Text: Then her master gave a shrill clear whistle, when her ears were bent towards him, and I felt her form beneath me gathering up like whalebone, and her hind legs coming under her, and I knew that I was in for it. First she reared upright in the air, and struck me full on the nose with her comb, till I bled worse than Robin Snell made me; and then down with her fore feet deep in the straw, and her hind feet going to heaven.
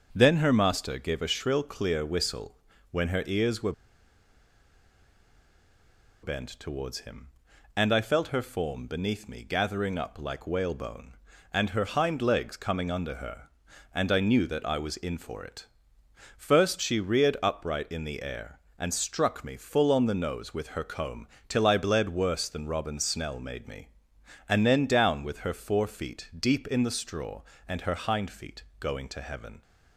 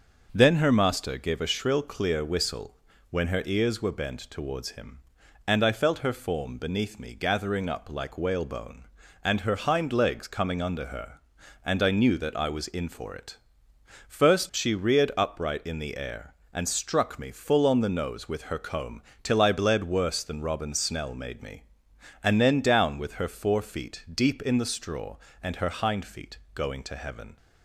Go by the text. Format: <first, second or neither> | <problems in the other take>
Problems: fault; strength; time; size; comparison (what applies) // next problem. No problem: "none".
second | starts louder than the rest; until 1.1 s; 6.5 dB; also in the second // pauses between "were" and "bent"; strong; at 3.7 s; 2.5 s long // pauses between "feet" and "going"; slight; at 28.6 s; 0.16 s long; slight in the second